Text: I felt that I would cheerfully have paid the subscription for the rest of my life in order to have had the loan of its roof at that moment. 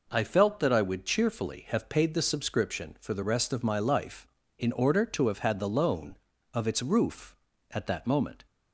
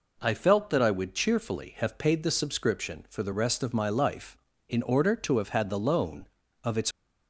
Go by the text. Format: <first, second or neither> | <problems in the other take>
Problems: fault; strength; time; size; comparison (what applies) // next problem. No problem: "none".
first | stops before "roof at that moment"; at 6.9 s